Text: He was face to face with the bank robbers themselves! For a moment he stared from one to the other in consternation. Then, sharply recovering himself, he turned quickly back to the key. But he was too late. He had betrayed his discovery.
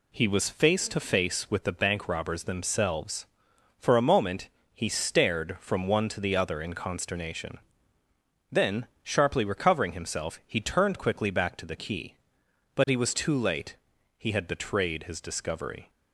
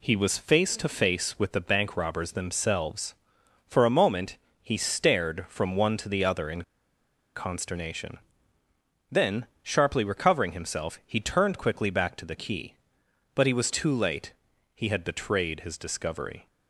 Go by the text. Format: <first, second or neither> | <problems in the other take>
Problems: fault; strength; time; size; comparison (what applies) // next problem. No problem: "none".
first | pauses between "moment" and "he"; slight; at 4.3 s; 0.26 s long; slight in the first // pauses between "in" and "consternation"; noticeable; at 6.6 s; 0.72 s long